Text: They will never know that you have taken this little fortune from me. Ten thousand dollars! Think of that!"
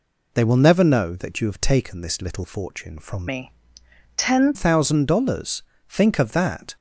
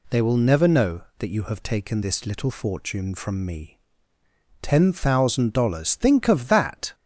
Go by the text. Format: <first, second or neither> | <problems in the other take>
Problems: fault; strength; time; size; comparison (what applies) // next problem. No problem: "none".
second | changes voice from "me" to "Ten"; from 3.2 to 4.5 s; 1.3 s long